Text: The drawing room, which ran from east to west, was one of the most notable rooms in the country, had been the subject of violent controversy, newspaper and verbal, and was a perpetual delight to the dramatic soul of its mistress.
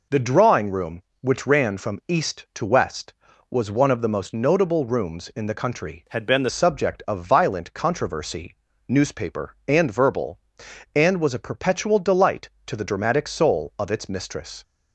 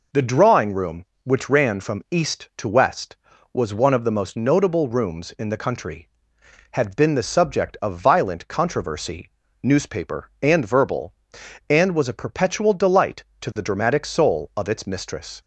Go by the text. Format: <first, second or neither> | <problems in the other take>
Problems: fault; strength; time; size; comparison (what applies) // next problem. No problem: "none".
second | changes voice from "had" to "the"; from 6.0 to 6.4 s; 0.4 s long